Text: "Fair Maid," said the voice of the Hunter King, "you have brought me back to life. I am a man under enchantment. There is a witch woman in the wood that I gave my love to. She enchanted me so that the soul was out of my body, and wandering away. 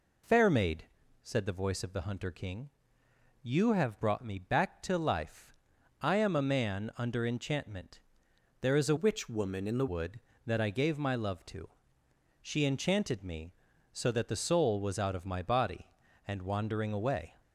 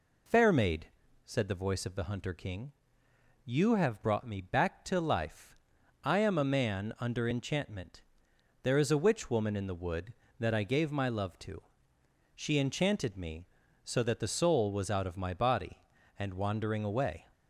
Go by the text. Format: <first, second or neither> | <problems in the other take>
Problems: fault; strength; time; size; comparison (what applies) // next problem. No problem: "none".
second | changes voice from "witch" to "the"; from 8.9 to 9.8 s; 0.9 s long